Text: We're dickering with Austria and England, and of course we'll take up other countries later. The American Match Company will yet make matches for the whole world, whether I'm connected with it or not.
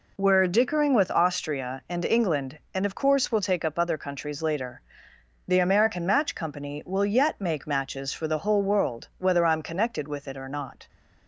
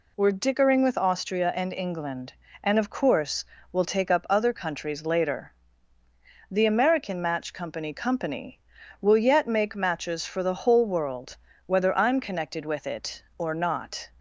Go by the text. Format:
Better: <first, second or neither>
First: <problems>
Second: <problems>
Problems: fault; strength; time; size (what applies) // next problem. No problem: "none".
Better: first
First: none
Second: pauses between "course" and "we'll"; slight; at 3.4 s; 0.28 s long // says "Company" twice; at 7.9 s